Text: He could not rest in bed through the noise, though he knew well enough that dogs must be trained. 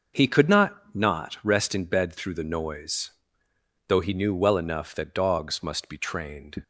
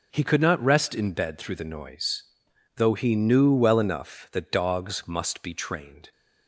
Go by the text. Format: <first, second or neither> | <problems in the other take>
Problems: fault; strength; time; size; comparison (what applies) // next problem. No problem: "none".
second | starts louder than the rest; until 1.3 s; 6 dB // says "not" twice; at 0.9 s